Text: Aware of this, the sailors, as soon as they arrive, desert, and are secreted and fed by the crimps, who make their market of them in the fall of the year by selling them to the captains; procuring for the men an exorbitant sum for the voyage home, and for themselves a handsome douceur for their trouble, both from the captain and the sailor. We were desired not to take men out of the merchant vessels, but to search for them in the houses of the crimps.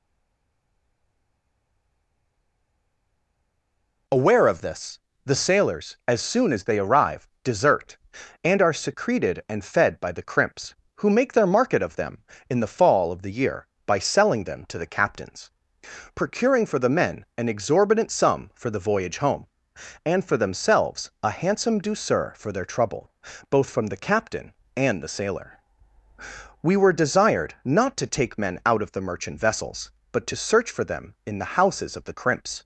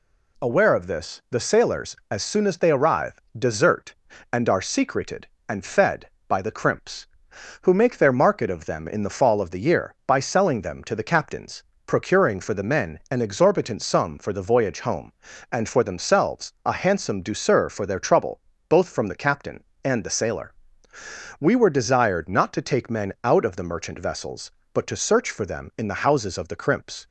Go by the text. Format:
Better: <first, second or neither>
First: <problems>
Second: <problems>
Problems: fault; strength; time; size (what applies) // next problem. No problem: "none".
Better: second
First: stays silent before the first word; strong; until 4.0 s; 4.0 s long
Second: none